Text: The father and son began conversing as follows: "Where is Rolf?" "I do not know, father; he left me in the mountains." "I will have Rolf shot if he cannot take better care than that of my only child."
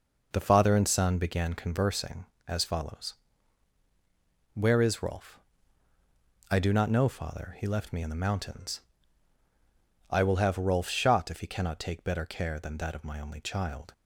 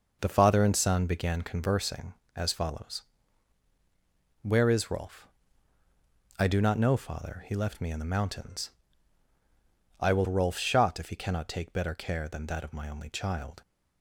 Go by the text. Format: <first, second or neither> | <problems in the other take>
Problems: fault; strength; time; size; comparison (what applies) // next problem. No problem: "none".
first | skips "have"; at 10.2 s